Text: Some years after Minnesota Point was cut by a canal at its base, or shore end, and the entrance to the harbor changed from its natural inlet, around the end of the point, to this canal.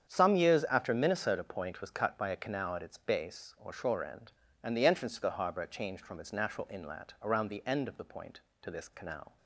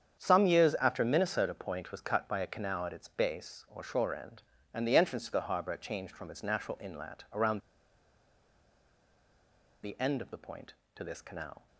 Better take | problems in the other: first | starts louder than the rest; strong; until 1.2 s; 8 dB; strong in the first // pauses between "around" and "the"; strong; at 7.5 s; 2.2 s long

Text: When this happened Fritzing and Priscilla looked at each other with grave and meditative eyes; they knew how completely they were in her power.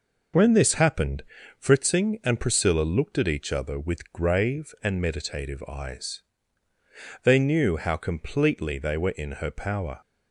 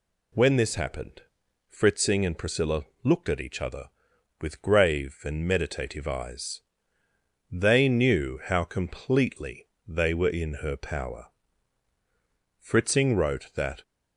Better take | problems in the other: first | pauses between "happened" and "Fritzing"; noticeable; at 1.2 s; 0.48 s long; also in the first // pauses between "Priscilla" and "looked"; slight; at 2.8 s; 0.20 s long // pauses between "completely" and "they"; slight; at 9.6 s; 0.20 s long // goes on to say "Fritzing wrote that"; noticeable; from 12.5 s on; 1.2 s long

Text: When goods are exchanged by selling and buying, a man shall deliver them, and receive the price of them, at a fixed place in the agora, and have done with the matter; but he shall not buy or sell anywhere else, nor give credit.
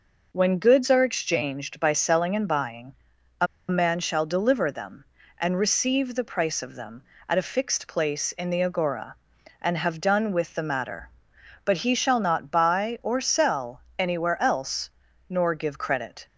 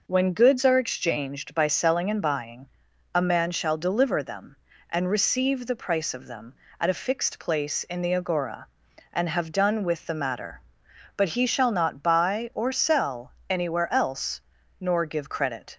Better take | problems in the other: second | pauses between "a" and "man"; slight; at 3.4 s; 0.23 s long

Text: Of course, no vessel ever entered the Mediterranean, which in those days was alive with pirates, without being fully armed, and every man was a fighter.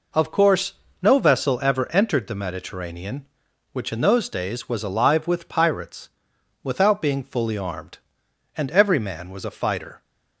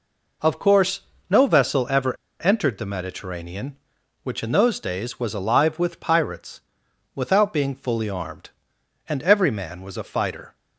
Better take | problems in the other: first | pauses between "ever" and "entered"; slight; at 2.1 s; 0.26 s long

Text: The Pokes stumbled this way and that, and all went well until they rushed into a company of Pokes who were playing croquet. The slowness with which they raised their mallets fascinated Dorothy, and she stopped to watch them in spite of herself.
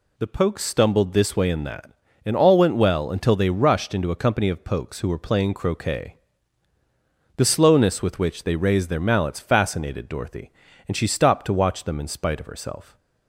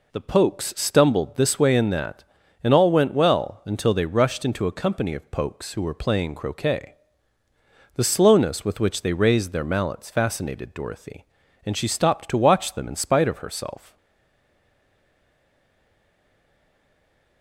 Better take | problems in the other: first | stays silent after the last word; strong; from 13.9 s on; 3.5 s long

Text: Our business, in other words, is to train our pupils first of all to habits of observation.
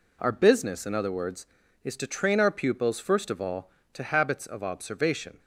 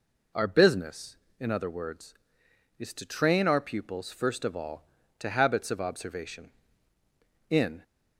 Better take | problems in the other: first | goes on to say "In"; slight; from 7.5 s on; 0.32 s long

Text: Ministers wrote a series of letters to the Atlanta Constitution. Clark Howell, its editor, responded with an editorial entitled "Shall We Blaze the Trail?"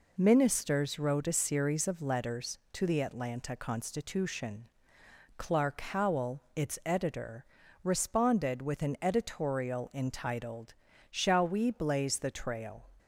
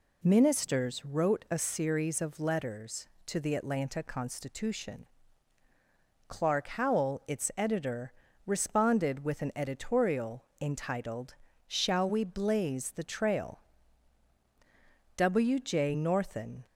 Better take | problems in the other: first | pauses between "editorial" and "entitled"; slight; at 10.4 s; 0.16 s long // pauses between "entitled" and "Shall"; slight; at 11.3 s; 0.32 s long; slight in the first // goes on to say "W J Northen"; from 15.1 s on; 1.4 s long

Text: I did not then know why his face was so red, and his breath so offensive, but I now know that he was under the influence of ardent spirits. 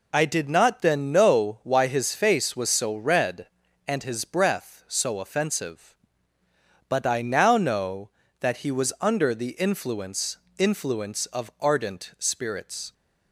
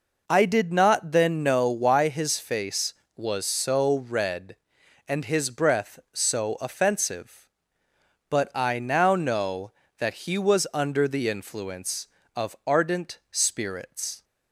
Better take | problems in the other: second | says "influence" twice; at 10.5 s

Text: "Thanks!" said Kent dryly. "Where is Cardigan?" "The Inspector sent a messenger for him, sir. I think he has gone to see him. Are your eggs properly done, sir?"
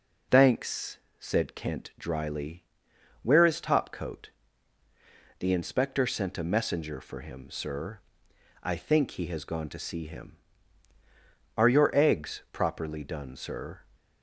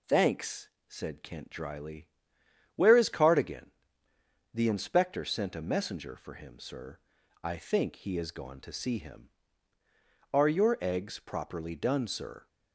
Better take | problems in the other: second | says "Topcoat" for "Cardigan"; at 3.6 s

